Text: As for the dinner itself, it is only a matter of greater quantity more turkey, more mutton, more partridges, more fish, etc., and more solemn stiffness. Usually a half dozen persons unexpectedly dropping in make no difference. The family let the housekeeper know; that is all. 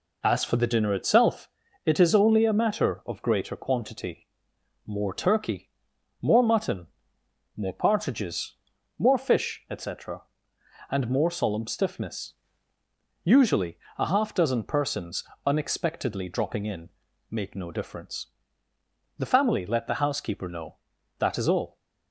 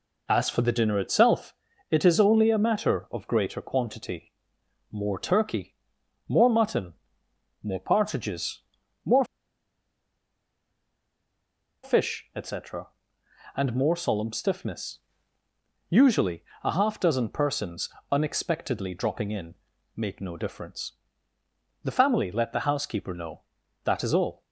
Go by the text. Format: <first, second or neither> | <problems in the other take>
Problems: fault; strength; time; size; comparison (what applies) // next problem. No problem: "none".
first | pauses between "quantity" and "more"; noticeable; at 4.3 s; 0.60 s long; noticeable in the first // pauses between "more" and "fish"; strong; at 9.2 s; 2.5 s long // pauses between "Usually" and "a"; slight; at 16.4 s; 0.20 s long; slight in the first // pauses between "persons" and "unexpectedly"; slight; at 17.8 s; 0.20 s long; slight in the first // pauses between "in" and "make"; at 19.5 s; 0.42 s long; also in the first